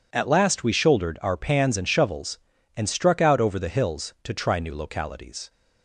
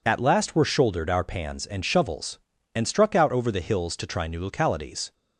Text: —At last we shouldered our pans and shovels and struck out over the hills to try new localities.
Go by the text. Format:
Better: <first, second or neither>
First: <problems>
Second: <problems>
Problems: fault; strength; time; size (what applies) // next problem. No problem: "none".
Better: first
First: none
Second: says "were" for "we"; at 0.5 s